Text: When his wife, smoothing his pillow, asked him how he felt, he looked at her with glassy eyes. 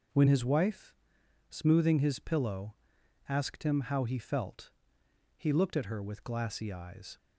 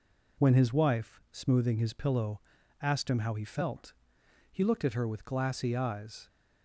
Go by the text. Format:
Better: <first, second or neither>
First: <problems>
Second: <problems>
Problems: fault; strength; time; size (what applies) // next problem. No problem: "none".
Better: neither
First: none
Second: none